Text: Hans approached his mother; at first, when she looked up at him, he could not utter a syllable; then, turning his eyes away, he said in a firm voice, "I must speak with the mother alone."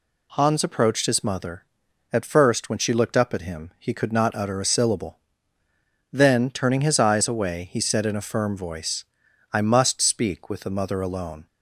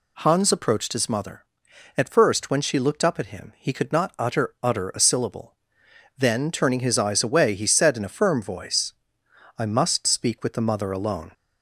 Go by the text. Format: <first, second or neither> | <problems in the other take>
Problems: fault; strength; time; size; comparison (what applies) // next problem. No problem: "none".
first | says "utter" twice; at 4.6 s